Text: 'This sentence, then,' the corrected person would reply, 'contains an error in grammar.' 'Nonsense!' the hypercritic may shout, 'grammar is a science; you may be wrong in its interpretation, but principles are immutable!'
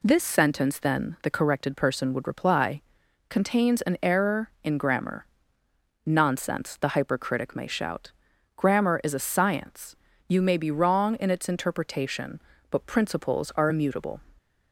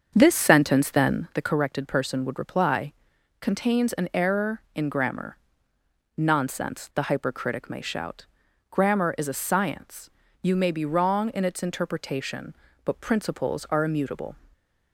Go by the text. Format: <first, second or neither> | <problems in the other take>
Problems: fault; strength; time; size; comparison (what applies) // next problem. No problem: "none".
first | starts louder than the rest; until 1.4 s; 7 dB // stays silent after the last word; slight; from 14.3 s on; 0.6 s long